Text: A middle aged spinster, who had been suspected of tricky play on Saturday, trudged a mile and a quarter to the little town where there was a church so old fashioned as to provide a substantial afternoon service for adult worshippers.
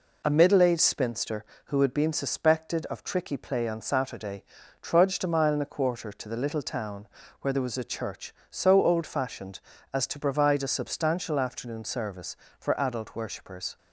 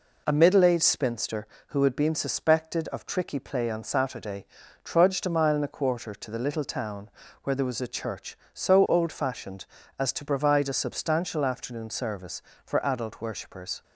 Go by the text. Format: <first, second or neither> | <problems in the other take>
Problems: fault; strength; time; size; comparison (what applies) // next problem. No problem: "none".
neither | pauses between "town" and "where"; slight; the same in both